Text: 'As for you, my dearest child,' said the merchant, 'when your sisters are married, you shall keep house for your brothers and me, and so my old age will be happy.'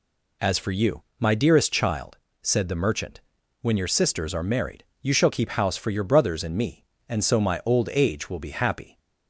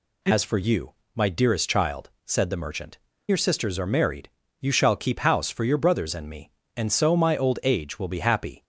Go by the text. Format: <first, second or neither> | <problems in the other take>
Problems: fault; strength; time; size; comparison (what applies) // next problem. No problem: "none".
first | skips "when"; at 3.1 s